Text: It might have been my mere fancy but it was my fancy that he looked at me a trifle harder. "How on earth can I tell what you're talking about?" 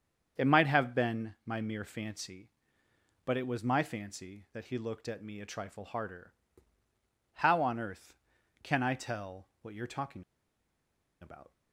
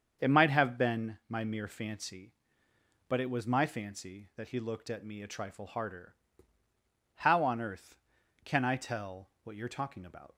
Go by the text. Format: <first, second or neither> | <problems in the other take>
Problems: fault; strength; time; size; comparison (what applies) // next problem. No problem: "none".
second | starts louder than the rest; strong; until 1.5 s; 7 dB; strong in the second // pauses between "talking" and "about"; at 10.2 s; 0.98 s long